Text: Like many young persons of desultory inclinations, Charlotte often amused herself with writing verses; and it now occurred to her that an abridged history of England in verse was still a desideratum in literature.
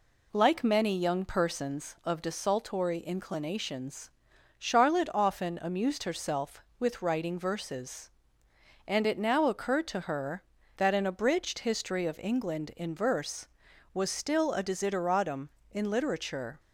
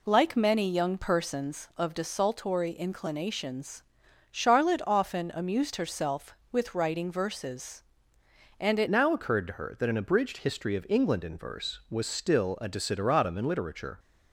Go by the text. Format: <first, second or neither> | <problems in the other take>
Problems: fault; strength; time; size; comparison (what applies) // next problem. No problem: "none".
first | changes voice at "now"; from 8.8 s on; 5.1 s long